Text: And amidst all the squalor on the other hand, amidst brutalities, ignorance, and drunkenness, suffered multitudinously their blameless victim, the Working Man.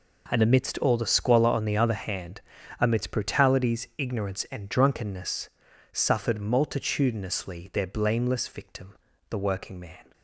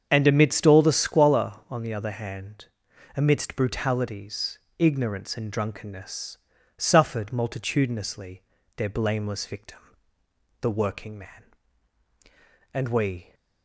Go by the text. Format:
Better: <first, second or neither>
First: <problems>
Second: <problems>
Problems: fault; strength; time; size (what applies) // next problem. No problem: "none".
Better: first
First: none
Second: starts louder than the rest; strong; until 1.1 s; 7.5 dB // pauses between "multitudinously" and "their"; slight; at 8.4 s; 0.34 s long // goes on to say "And we"; noticeable; from 12.7 s on; 0.62 s long